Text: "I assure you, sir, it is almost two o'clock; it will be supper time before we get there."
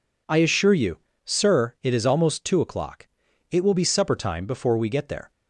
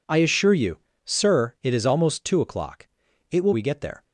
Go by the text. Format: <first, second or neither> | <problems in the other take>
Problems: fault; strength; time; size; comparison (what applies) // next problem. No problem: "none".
first | skips "be supper time before"; at 3.5 s